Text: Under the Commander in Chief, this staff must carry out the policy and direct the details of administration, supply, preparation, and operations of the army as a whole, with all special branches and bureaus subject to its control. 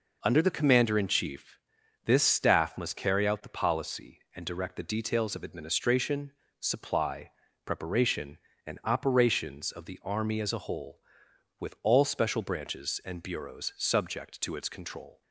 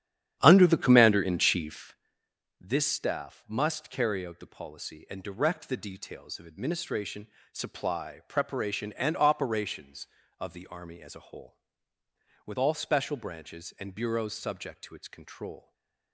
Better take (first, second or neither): first